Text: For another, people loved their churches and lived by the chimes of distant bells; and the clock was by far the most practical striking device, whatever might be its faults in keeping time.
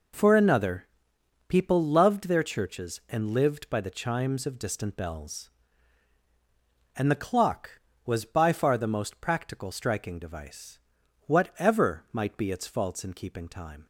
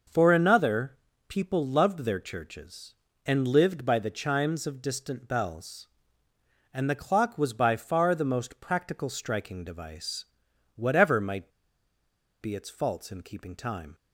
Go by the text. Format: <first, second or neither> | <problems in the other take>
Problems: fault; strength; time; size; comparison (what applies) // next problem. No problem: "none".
first | pauses between "might" and "be"; noticeable; at 11.5 s; 0.91 s long